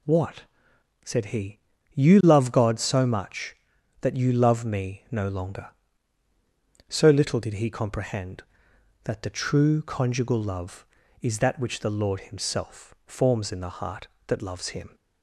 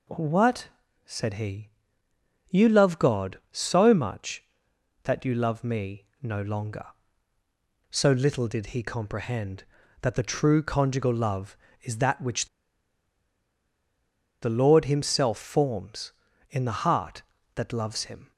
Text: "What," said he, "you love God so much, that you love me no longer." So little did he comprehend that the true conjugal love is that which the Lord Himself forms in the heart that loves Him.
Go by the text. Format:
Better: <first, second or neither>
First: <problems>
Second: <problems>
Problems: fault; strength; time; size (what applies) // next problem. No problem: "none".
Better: first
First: none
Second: pauses between "me" and "no"; slight; at 6.0 s; 0.16 s long // pauses between "which" and "the"; strong; at 12.4 s; 1.9 s long